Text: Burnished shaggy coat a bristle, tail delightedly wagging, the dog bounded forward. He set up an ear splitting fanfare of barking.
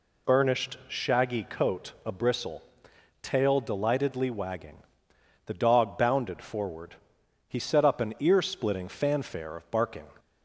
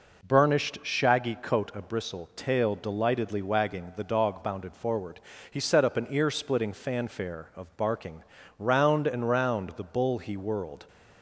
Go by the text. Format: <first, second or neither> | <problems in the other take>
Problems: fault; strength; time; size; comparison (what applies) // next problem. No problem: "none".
first | goes on to say "Round and round the bull he whirled"; strong; from 8.5 s on; 2.2 s long